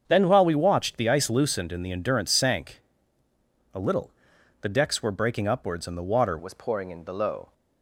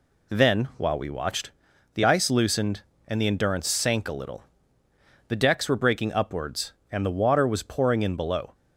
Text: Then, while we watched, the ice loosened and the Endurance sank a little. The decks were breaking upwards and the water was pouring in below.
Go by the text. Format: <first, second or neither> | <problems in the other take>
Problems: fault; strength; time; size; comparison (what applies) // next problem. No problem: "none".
second | starts louder than the rest; strong; until 1.0 s; 7.5 dB // pauses between "sank" and "a"; noticeable; at 2.8 s; 0.92 s long // changes voice at "was"; from 6.3 s on; 1.2 s long